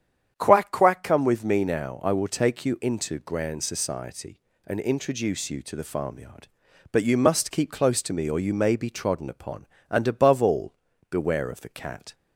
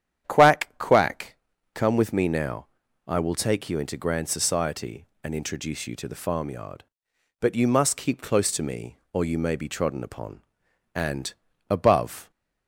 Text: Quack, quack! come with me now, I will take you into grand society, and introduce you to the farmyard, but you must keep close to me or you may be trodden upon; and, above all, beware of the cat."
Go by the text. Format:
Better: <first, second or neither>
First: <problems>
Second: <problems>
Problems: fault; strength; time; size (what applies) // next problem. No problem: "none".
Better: first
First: starts louder than the rest; strong; until 1.3 s; 8.5 dB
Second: starts louder than the rest; strong; until 1.3 s; 9.5 dB // stops before "all beware of the cat"; at 12.3 s